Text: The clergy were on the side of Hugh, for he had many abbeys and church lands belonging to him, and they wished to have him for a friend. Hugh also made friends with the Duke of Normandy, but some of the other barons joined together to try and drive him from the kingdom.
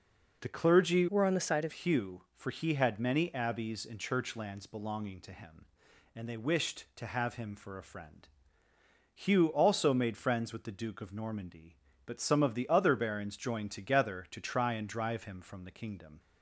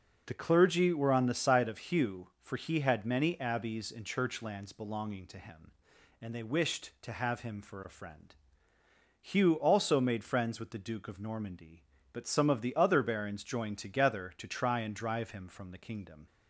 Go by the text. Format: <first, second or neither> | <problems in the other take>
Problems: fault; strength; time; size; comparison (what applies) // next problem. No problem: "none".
second | changes voice from "were" to "of"; from 1.1 to 1.7 s; 0.6 s long